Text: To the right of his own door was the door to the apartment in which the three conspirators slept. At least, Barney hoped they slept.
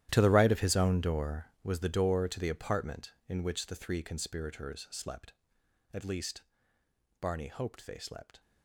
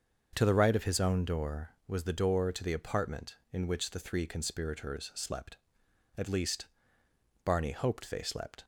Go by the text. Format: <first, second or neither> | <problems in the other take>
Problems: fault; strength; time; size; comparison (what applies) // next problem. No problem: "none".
second | gets quieter; strong; throughout; 16 dB // starts louder than the rest; strong; until 1.1 s; 12.5 dB; also in the second